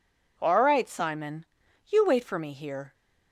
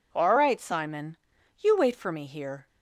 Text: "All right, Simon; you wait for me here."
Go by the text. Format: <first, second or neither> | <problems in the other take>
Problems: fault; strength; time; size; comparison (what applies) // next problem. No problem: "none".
neither | none